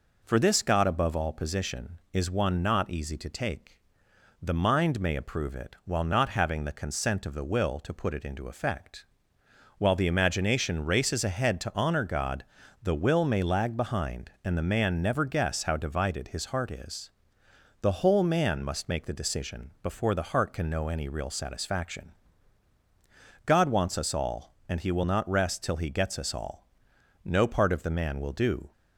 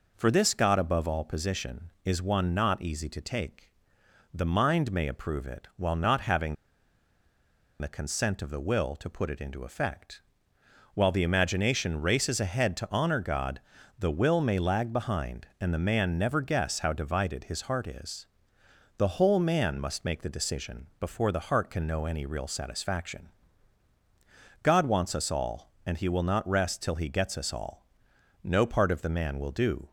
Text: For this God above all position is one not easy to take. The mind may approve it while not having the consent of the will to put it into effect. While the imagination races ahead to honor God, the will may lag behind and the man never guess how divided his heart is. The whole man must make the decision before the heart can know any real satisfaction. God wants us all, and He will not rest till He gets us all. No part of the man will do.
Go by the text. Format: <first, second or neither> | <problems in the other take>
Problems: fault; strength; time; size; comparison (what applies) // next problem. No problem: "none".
first | pauses between "having" and "the"; strong; at 6.5 s; 1.2 s long